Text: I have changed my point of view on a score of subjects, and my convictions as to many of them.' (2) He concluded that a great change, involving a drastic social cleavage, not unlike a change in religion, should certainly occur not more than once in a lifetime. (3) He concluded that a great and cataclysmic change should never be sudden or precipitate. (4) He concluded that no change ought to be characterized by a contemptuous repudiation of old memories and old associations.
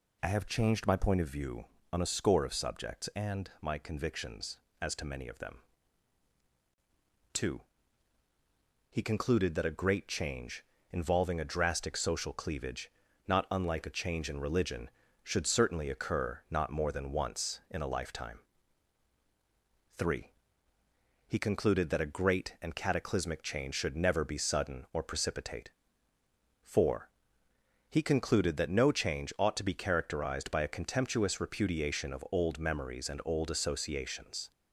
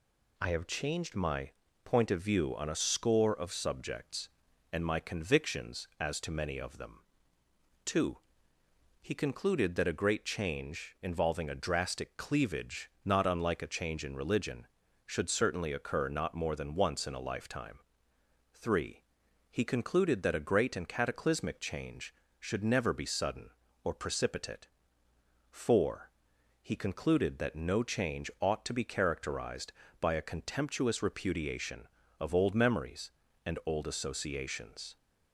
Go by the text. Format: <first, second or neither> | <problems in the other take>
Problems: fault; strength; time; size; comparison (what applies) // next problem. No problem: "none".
first | pauses between "my" and "point"; slight; at 1.5 s; 0.32 s long // skips "social"; at 12.1 s